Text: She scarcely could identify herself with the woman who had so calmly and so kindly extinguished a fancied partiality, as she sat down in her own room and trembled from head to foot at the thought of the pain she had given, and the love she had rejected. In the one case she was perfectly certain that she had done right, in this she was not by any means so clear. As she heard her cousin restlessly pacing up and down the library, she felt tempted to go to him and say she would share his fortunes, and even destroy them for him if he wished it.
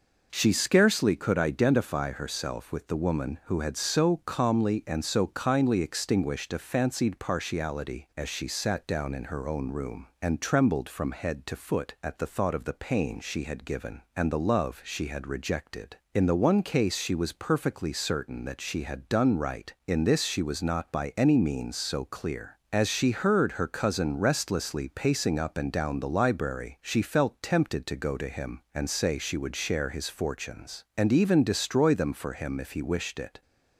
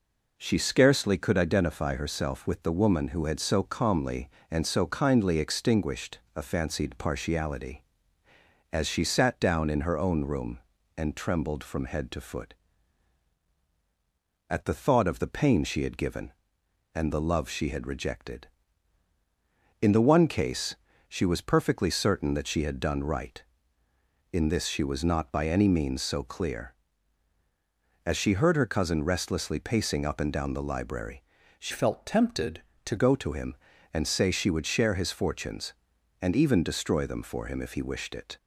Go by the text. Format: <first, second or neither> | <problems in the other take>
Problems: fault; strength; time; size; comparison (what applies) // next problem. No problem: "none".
first | pauses between "extinguished" and "a"; slight; at 6.1 s; 0.16 s long // pauses between "case" and "she"; slight; at 20.7 s; 0.32 s long // changes voice from "felt" to "to"; from 31.7 to 32.9 s; 1.2 s long